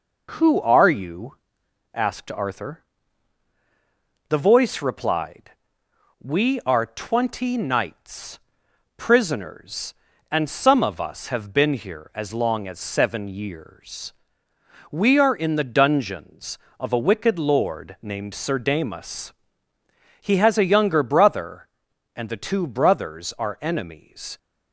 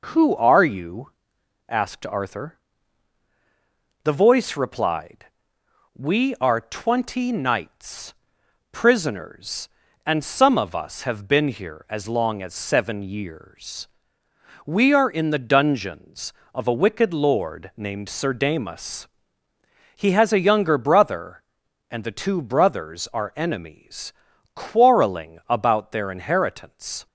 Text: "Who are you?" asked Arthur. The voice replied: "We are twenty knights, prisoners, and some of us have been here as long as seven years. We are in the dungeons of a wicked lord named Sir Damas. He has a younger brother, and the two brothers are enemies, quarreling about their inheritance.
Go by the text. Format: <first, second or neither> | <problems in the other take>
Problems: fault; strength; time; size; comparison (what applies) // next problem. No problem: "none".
second | stops before "quarreling about their inheritance"; at 24.3 s